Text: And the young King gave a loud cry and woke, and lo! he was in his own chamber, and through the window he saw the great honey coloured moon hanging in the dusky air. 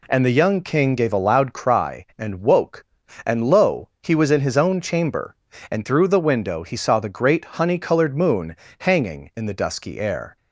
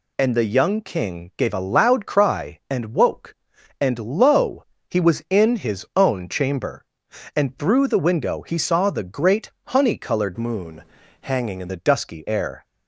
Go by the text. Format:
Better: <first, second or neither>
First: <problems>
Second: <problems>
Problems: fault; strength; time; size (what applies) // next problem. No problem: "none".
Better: first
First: pauses between "moon" and "hanging"; slight; at 8.5 s; 0.24 s long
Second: changes voice from "moon" to "in"; from 10.3 to 11.6 s; 1.3 s long // pauses between "moon" and "hanging"; at 10.8 s; 0.40 s long